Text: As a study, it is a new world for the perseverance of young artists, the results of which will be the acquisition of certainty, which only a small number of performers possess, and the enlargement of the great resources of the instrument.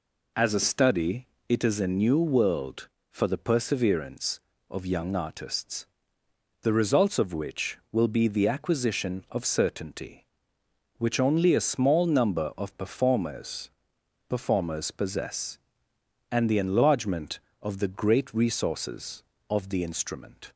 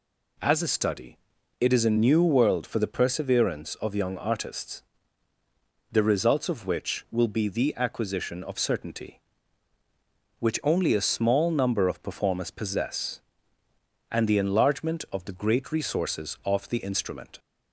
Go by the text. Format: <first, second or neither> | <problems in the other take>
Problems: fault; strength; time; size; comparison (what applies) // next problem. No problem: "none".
second | says "performers" twice; at 14.2 s